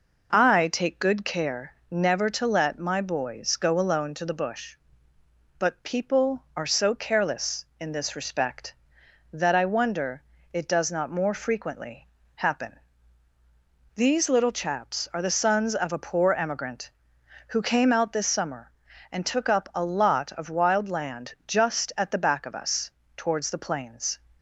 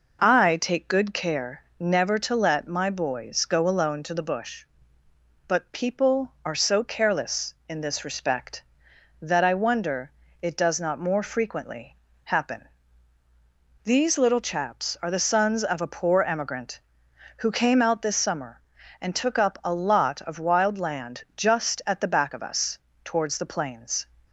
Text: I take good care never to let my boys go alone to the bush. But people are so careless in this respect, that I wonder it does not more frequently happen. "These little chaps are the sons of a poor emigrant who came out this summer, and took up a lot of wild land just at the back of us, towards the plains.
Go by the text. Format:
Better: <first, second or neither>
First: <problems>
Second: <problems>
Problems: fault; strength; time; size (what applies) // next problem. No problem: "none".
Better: neither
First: pauses between "care" and "never"; slight; at 1.7 s; 0.18 s long // pauses between "wonder" and "it"; slight; at 10.2 s; 0.30 s long // pauses between "frequently" and "happen"; slight; at 12.0 s; 0.28 s long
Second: pauses between "care" and "never"; slight; at 1.6 s; 0.18 s long // pauses between "wonder" and "it"; slight; at 10.1 s; 0.30 s long // pauses between "frequently" and "happen"; slight; at 11.9 s; 0.28 s long